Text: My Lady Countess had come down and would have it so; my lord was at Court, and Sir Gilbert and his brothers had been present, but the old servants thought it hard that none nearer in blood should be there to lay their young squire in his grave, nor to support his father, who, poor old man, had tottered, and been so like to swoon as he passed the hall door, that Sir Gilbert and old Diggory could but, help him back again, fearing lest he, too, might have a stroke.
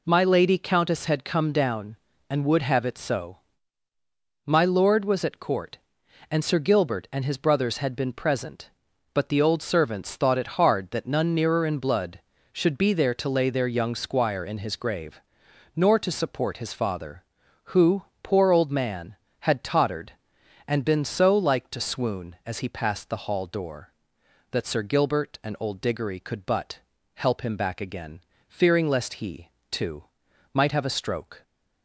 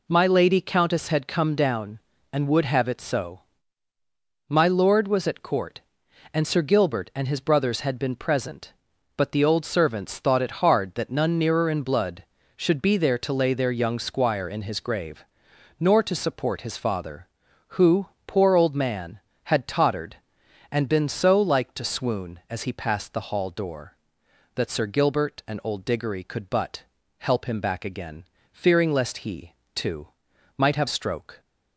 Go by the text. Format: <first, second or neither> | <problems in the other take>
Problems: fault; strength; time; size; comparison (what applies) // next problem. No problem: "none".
first | skips "a"; at 30.8 s